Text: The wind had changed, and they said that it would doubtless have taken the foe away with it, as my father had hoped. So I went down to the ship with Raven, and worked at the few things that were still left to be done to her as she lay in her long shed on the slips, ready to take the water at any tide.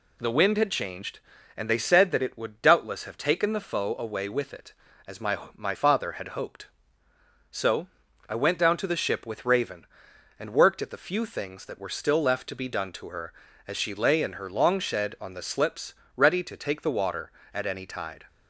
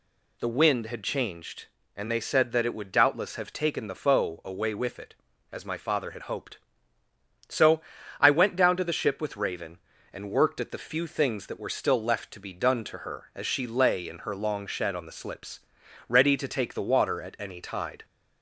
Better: second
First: says "my" twice; at 5.5 s // pauses between "So" and "I"; at 7.8 s; 0.42 s long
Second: pauses between "So" and "I"; at 7.8 s; 0.38 s long

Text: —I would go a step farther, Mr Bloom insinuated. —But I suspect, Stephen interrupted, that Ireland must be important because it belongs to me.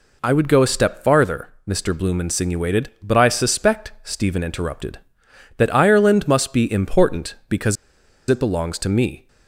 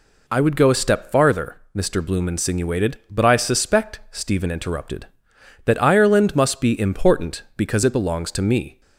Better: second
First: pauses between "because" and "it"; noticeable; at 7.7 s; 0.53 s long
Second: none

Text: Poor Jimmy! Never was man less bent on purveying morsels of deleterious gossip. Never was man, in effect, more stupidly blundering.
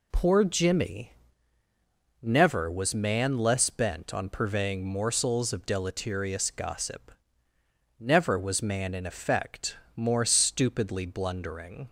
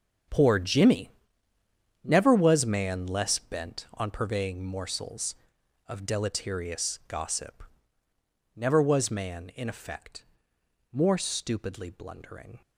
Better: first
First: none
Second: gets quieter; strong; throughout; 13 dB

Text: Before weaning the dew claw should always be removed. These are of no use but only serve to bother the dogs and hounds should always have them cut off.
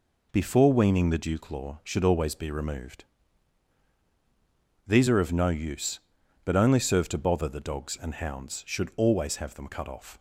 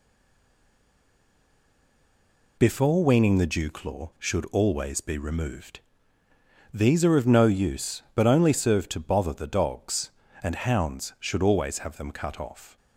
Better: first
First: none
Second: stays silent before the first word; strong; until 2.5 s; 2.5 s long

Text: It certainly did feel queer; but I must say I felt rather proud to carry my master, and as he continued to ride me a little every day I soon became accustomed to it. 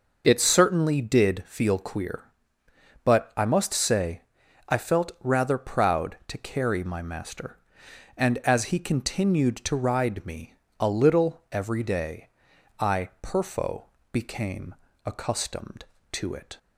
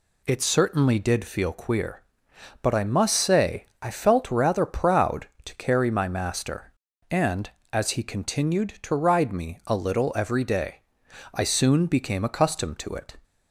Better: second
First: pauses between "say" and "I"; noticeable; at 4.2 s; 0.46 s long // pauses between "me" and "a"; slight; at 10.5 s; 0.26 s long // pauses between "day" and "I"; noticeable; at 12.2 s; 0.52 s long // says "perfo" for "soon"; at 13.2 s // pauses between "became" and "accustomed"; slight; at 14.7 s; 0.32 s long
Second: pauses between "day" and "I"; noticeable; at 10.8 s; 0.52 s long

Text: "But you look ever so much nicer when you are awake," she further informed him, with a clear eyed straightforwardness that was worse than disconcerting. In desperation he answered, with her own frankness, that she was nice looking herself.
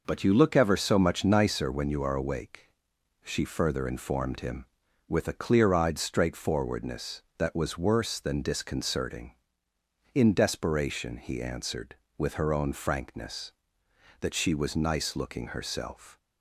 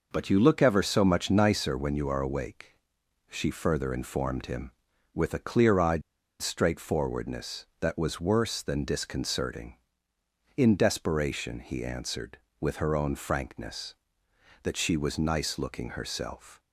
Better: first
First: none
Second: pauses between "eyed" and "straightforwardness"; at 6.0 s; 0.39 s long

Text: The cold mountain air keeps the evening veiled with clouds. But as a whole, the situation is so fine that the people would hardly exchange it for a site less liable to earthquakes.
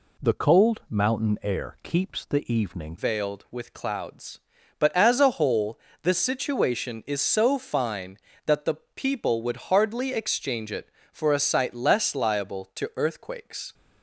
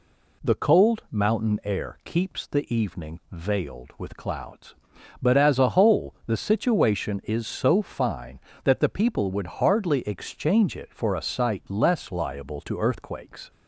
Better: second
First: changes voice at "veiled"; from 2.9 s on; 10.8 s long // pauses between "the" and "people"; slight; at 8.7 s; 0.18 s long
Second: none

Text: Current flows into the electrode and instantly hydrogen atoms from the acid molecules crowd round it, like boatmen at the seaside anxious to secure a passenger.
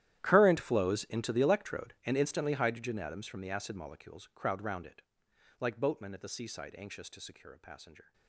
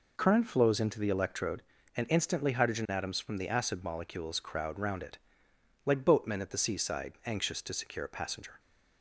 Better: second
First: gets quieter; strong; throughout; 19.5 dB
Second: none

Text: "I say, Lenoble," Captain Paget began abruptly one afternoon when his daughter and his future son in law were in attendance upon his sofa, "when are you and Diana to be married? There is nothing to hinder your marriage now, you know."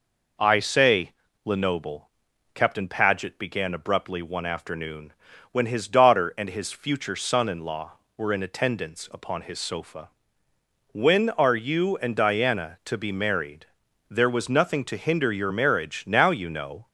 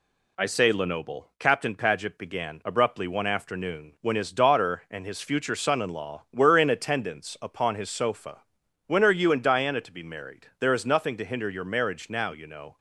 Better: second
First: pauses between "afternoon" and "when"; at 5.1 s; 0.40 s long // says "was" for "is"; at 14.2 s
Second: none

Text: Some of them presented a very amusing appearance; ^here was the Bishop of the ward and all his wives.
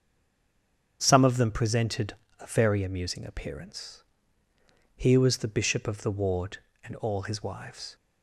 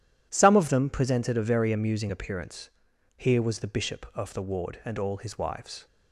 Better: second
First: stays silent before the first word; until 0.9 s; 0.9 s long // starts louder than the rest; strong; until 2.0 s; 7.5 dB // pauses between "presented" and "a"; slight; at 2.1 s; 0.26 s long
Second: none

